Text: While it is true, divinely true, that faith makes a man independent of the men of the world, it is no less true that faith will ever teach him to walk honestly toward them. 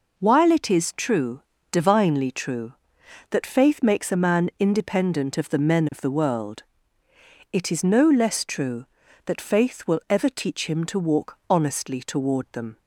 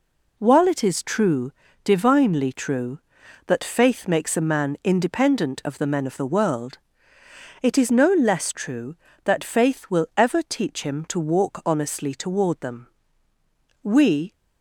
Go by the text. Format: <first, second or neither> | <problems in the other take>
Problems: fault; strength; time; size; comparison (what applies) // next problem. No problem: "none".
first | goes on to say "We"; from 13.8 s on; 0.50 s long